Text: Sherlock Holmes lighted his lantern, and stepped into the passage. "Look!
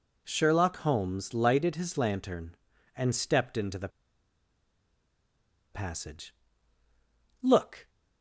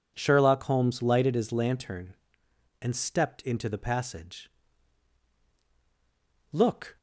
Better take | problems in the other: second | pauses between "the" and "passage"; strong; at 3.9 s; 1.8 s long

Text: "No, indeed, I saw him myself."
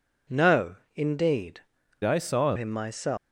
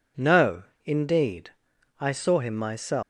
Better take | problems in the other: second | changes voice from "I" to "saw"; from 2.0 to 2.5 s; 0.5 s long

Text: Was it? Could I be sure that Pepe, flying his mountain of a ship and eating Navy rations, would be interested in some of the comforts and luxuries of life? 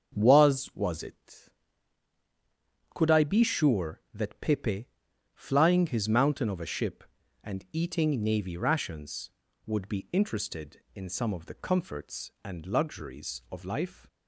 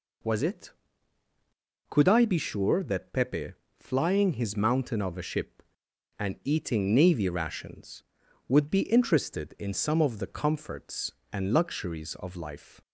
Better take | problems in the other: second | starts louder than the rest; until 1.2 s; 7 dB // says "Was" twice; at 0.7 s

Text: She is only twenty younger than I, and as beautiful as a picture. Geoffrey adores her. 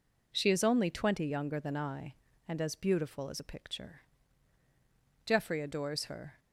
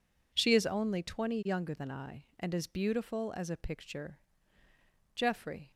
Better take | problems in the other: first | stops before "adores her"; at 5.7 s

